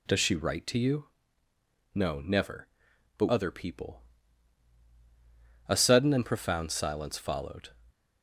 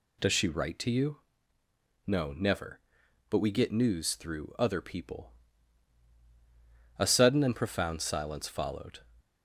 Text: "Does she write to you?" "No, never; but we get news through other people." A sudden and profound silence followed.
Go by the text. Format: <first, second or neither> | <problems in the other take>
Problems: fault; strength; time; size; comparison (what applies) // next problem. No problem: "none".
second | skips "we get news through"; at 3.2 s